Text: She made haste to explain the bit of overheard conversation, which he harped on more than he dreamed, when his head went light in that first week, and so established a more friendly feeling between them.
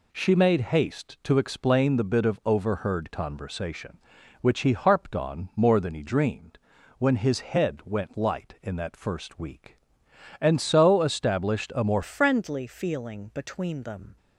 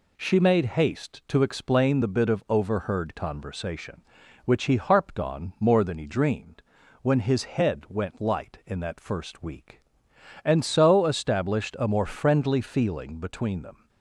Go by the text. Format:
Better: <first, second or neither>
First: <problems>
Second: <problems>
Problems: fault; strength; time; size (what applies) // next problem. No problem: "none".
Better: second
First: changes voice at "friendly"; from 12.0 s on; 2.1 s long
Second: none